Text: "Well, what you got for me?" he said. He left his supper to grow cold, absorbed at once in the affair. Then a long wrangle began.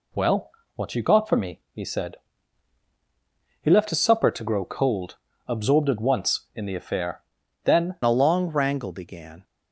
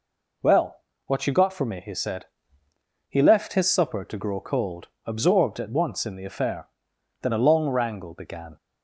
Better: second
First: changes voice at "a"; from 8.0 s on; 1.4 s long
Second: none

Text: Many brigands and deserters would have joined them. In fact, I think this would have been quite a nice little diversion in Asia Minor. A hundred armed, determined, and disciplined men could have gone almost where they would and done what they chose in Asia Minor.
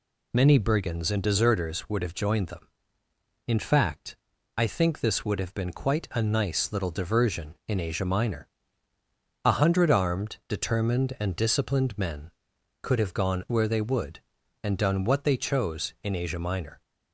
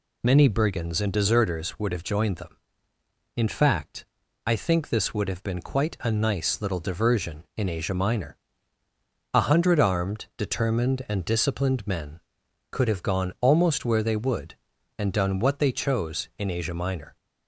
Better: second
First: skips "almost"; at 13.4 s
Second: none

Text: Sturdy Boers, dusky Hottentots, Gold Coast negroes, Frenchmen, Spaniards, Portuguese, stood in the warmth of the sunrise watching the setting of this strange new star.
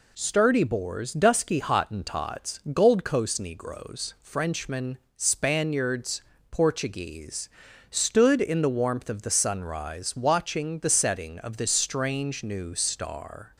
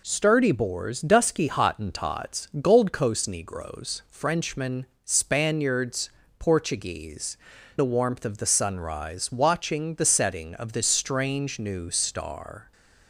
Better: first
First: none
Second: skips "stood in"; at 7.5 s

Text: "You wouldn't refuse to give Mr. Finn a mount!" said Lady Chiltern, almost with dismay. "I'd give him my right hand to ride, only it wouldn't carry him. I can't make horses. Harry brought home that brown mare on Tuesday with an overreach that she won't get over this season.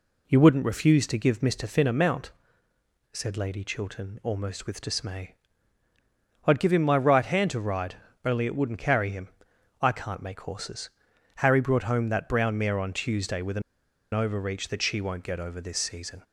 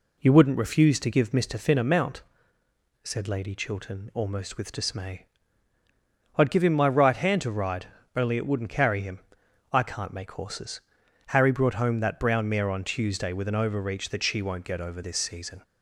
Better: second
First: pauses between "an" and "overreach"; noticeable; at 13.6 s; 0.52 s long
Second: none

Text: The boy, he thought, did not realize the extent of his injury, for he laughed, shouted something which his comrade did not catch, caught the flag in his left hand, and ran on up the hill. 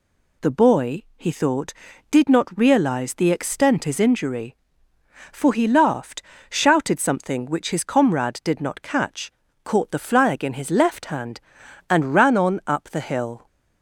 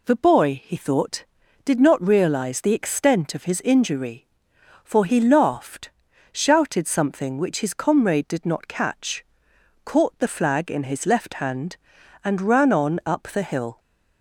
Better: second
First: skips "of"; at 3.8 s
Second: none

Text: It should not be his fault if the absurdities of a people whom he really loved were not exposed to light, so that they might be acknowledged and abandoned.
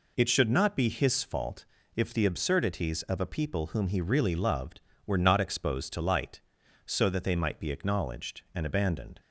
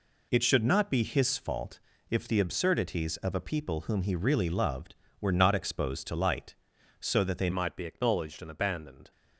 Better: first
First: pauses between "fault" and "if"; slight; at 1.6 s; 0.30 s long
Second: pauses between "fault" and "if"; slight; at 1.7 s; 0.30 s long // changes voice at "might"; from 7.5 s on; 1.6 s long

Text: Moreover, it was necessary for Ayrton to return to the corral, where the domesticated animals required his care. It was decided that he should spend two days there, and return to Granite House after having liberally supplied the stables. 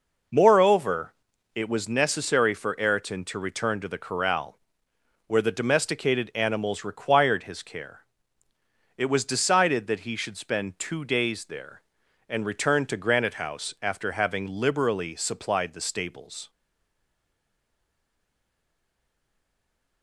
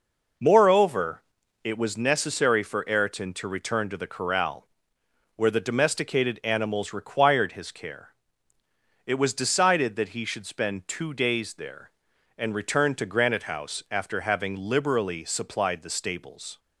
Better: second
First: stays silent after the last word; strong; from 16.4 s on; 3.6 s long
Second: none

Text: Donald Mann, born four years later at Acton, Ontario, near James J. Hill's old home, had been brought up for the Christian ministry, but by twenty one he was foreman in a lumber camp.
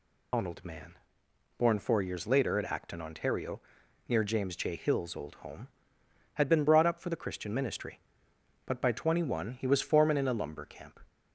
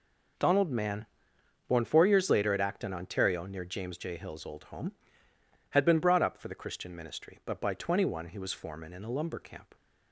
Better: second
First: loses the start of "Donald"; at 0.3 s; 80 ms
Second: none

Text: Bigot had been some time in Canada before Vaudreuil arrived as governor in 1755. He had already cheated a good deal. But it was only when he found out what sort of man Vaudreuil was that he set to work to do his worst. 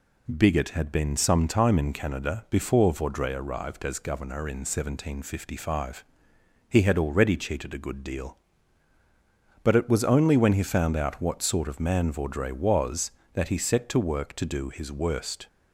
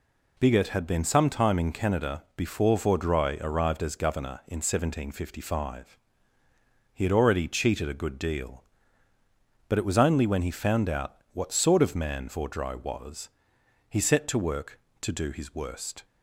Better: first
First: none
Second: pauses between "out" and "what"; slight; at 11.1 s; 0.18 s long // skips "that"; at 13.5 s

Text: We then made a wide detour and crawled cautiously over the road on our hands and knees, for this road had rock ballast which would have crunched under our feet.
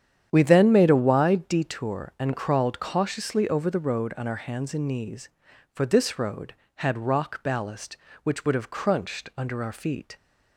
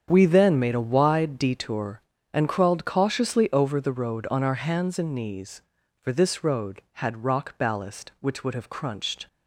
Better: first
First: starts louder than the rest; strong; until 1.3 s; 9 dB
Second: starts louder than the rest; strong; until 1.1 s; 7.5 dB // stops before "under our feet"; at 9.2 s

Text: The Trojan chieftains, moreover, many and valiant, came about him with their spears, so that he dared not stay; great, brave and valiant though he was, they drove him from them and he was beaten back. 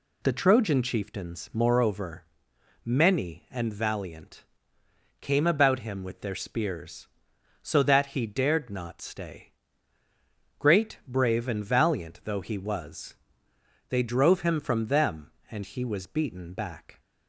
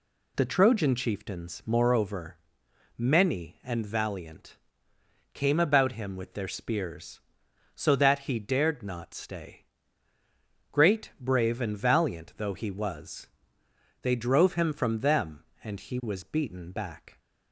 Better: neither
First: none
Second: none

